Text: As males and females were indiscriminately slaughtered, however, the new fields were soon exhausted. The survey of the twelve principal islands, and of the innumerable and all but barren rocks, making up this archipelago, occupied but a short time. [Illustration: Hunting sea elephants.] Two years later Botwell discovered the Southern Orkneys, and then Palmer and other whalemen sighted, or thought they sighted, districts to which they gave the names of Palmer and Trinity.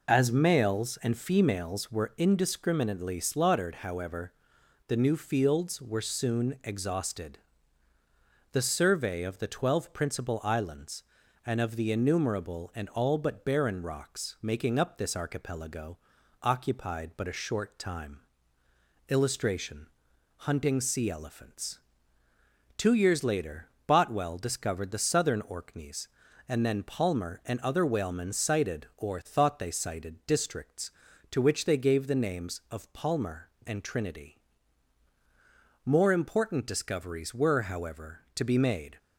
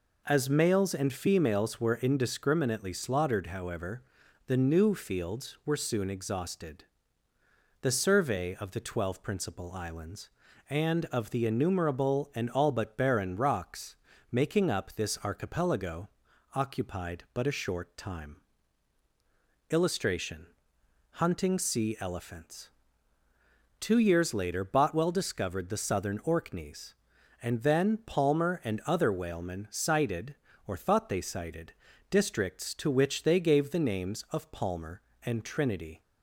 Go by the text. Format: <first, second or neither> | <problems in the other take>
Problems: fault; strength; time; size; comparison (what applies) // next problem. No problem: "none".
second | pauses between "later" and "Botwell"; slight; at 23.6 s; 0.20 s long // goes on to say "More important discoveries were however to be made"; strong; from 35.8 s on; 3.1 s long